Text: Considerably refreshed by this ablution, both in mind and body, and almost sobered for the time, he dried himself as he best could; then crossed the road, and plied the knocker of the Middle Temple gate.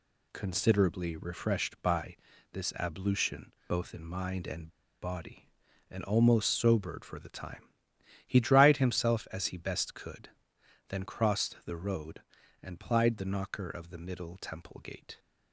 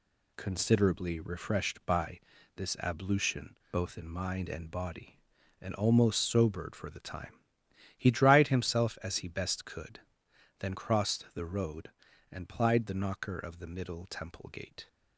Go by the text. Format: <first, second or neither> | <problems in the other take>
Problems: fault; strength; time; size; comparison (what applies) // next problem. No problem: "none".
second | pauses between "by" and "this"; slight; at 2.1 s; 0.36 s long; slight in the second // pauses between "and" and "body"; slight; at 4.6 s; 0.32 s long